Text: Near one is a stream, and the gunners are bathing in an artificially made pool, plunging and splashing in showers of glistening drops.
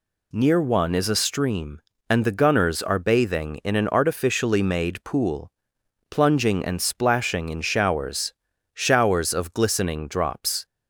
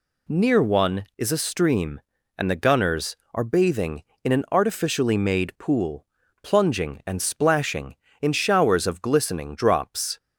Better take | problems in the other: second | says "showers" twice; at 8.7 s

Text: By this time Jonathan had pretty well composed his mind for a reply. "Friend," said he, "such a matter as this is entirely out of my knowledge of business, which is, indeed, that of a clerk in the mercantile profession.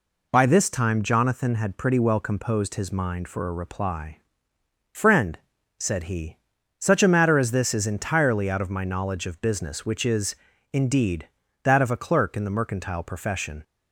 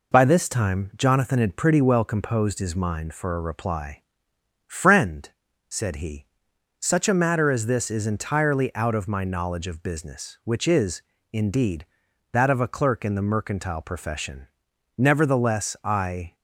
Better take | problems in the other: first | goes on to say "Nevertheless I"; from 14.9 s on; 1.3 s long

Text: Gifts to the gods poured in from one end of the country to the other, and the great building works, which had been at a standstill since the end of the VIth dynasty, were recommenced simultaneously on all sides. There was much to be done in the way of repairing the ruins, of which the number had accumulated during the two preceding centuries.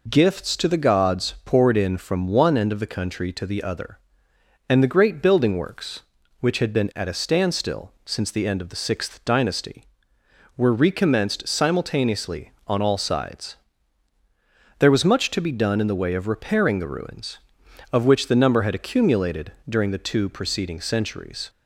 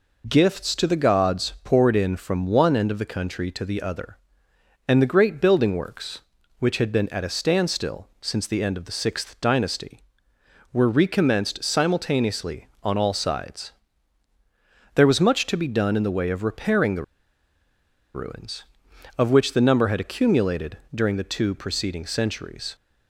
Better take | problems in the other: first | pauses between "the" and "ruins"; at 17.0 s; 1.1 s long // pauses between "accumulated" and "during"; slight; at 20.7 s; 0.16 s long; slight in the first

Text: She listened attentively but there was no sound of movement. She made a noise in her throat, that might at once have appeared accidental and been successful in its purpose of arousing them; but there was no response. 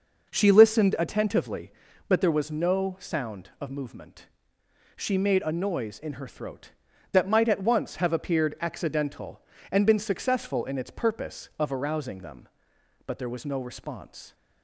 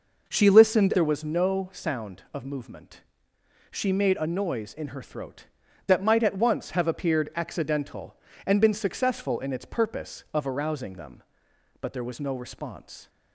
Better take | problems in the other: first | skips "attentively but"; at 0.9 s

